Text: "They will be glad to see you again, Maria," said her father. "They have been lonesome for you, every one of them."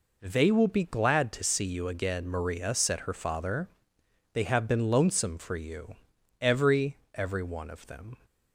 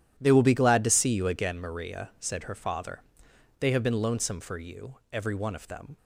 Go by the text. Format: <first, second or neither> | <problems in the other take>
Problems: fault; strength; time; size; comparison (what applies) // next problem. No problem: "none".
second | says "every" twice; at 7.1 s